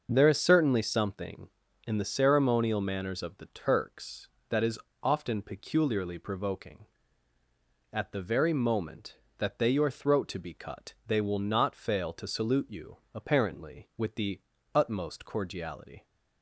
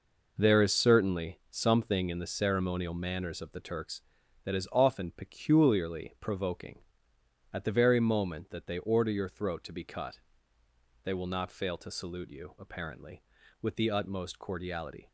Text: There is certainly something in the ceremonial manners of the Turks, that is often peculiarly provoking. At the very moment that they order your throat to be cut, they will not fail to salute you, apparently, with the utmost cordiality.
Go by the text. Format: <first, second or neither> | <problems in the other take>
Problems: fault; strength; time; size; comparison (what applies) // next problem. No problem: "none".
second | starts louder than the rest; noticeable; until 1.1 s; 6 dB // pauses between "is" and "often"; slight; at 4.7 s; 0.24 s long // skips "order"; at 9.7 s // pauses between "the" and "utmost"; slight; at 14.4 s; 0.34 s long